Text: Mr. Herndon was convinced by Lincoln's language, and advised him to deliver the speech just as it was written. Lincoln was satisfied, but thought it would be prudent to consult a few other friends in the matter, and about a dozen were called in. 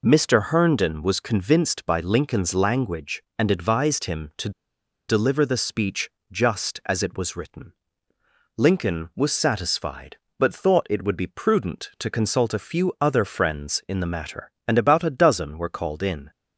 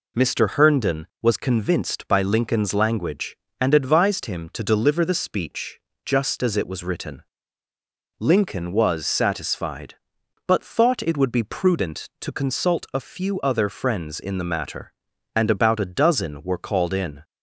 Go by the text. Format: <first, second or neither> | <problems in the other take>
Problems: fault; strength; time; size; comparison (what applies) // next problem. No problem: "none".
second | pauses between "to" and "deliver"; noticeable; at 4.5 s; 0.58 s long // pauses between "speech" and "just"; slight; at 6.1 s; 0.20 s long; slight in the second